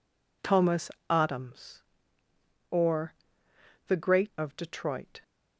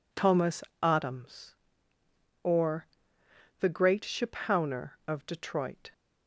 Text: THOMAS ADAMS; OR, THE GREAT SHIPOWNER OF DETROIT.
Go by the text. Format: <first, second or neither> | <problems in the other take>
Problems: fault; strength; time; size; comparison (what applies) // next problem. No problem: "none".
second | pauses between "THOMAS" and "ADAMS"; slight; at 0.8 s; 0.20 s long; slight in the second // skips "SHIPOWNER"; at 4.3 s